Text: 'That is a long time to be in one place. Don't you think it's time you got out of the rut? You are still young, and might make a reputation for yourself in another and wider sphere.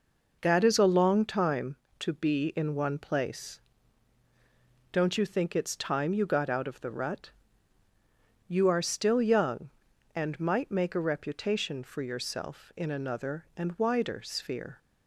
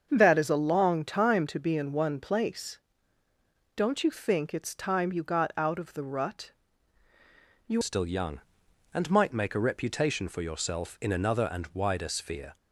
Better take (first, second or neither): first